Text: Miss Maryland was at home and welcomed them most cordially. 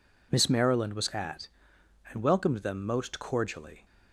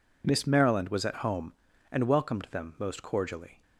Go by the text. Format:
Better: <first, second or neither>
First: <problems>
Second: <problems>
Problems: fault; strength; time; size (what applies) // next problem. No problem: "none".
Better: second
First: skips "home"; at 1.7 s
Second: none